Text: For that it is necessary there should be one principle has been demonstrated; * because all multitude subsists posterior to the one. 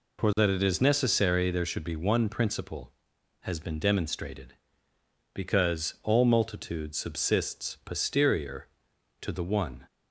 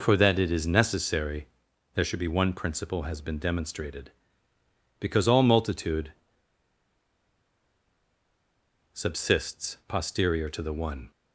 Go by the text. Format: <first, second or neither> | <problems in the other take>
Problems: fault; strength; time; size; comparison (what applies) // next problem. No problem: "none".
first | pauses between "necessary" and "there"; noticeable; at 1.4 s; 0.48 s long // pauses between "multitude" and "subsists"; strong; at 6.1 s; 2.8 s long